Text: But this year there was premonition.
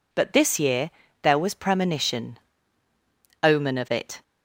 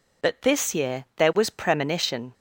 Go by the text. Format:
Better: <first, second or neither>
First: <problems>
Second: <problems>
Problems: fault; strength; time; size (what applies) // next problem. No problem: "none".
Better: second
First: pauses between "year" and "there"; slight; at 0.9 s; 0.30 s long // goes on to say "Omen of it"; noticeable; from 3.4 s on; 0.79 s long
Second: none